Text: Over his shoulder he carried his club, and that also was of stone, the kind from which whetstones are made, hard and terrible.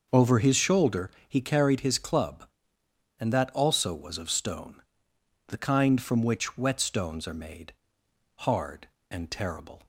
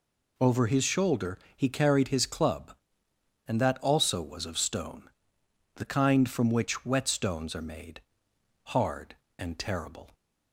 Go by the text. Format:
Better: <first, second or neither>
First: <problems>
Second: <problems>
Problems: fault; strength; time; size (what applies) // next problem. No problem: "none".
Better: second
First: starts louder than the rest; noticeable; until 1.1 s; 6 dB // pauses between "shoulder" and "he"; slight; at 1.1 s; 0.18 s long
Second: pauses between "shoulder" and "he"; slight; at 1.3 s; 0.18 s long